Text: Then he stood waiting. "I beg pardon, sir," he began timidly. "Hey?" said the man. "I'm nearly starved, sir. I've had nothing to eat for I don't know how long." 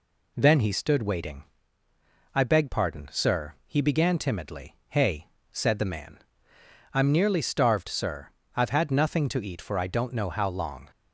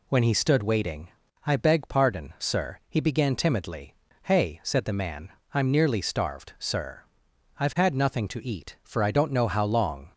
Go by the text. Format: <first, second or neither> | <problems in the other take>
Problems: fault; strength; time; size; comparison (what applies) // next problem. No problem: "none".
first | says "When" for "Then"; at 0.0 s